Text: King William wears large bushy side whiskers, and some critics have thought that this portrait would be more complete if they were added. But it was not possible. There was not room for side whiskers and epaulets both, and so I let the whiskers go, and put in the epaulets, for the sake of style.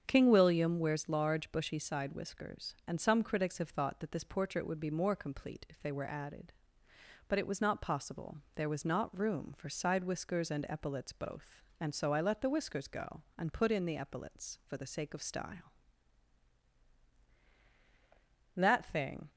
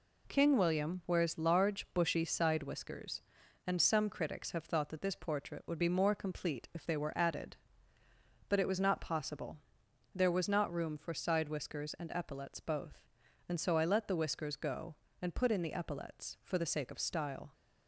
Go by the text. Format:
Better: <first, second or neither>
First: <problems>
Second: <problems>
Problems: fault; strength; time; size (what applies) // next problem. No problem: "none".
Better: second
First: starts louder than the rest; strong; until 1.0 s; 7.5 dB // goes on to say "That thing"; noticeable; from 18.5 s on; 0.74 s long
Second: none